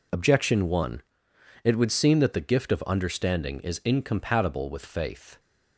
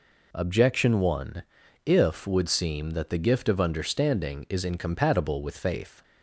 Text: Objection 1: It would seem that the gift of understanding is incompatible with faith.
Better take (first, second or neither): first